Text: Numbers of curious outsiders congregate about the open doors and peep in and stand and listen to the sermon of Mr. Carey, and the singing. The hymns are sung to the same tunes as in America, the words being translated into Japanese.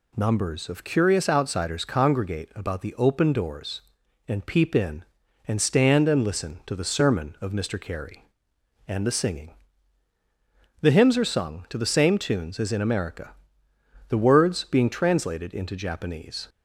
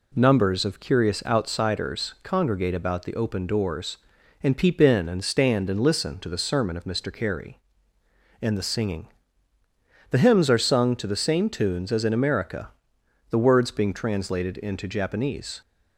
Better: neither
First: none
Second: none

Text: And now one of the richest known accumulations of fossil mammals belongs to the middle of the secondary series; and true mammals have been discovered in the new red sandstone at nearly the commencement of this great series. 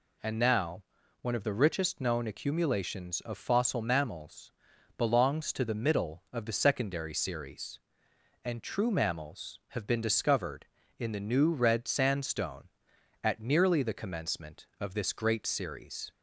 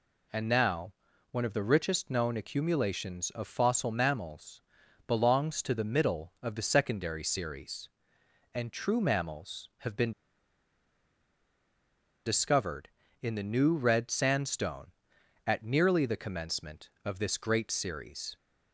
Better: first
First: pauses between "now" and "one"; at 0.8 s; 0.40 s long // pauses between "mammals" and "belongs"; noticeable; at 4.5 s; 0.46 s long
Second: pauses between "now" and "one"; at 0.9 s; 0.40 s long // pauses between "mammals" and "belongs"; noticeable; at 4.5 s; 0.46 s long // pauses between "been" and "discovered"; strong; at 10.1 s; 2.1 s long

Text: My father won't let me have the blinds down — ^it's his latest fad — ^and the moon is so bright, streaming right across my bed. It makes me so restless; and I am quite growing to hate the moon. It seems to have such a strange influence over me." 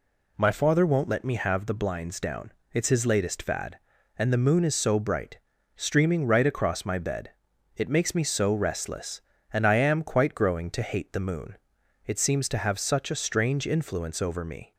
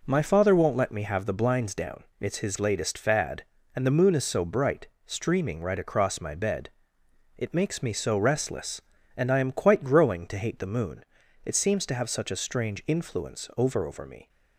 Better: first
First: none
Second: says "over" twice; at 13.8 s

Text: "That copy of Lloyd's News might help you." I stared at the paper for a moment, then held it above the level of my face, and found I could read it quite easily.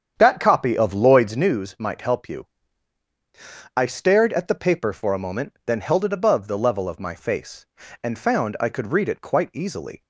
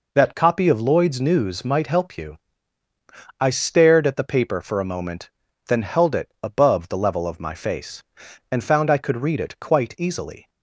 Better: second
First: starts louder than the rest; strong; until 1.5 s; 8 dB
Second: none

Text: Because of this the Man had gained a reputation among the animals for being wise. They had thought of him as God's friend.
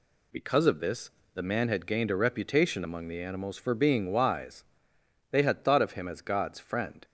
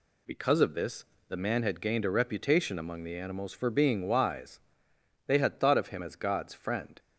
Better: neither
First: pauses between "this" and "the"; slight; at 1.0 s; 0.24 s long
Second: pauses between "this" and "the"; slight; at 1.0 s; 0.24 s long

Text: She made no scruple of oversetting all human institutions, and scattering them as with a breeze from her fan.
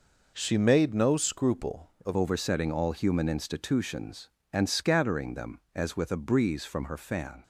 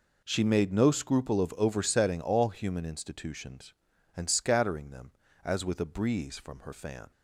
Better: second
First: changes voice at "oversetting"; from 2.1 s on; 5.3 s long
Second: none

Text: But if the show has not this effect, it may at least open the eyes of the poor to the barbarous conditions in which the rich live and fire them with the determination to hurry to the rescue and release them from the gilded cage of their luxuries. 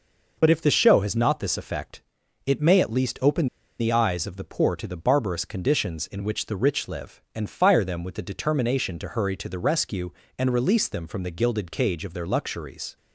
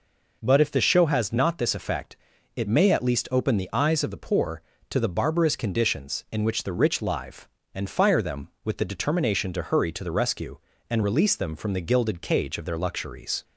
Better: second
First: pauses between "open" and "the"; slight; at 3.4 s; 0.32 s long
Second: none

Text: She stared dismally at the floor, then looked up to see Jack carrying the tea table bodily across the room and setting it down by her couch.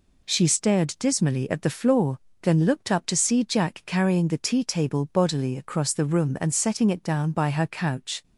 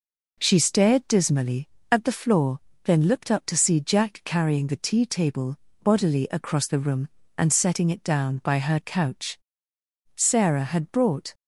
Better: first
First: none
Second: pauses between "table" and "bodily"; slight; at 5.5 s; 0.24 s long // goes on to say "Sarah had brought"; noticeable; from 10.1 s on; 1.1 s long

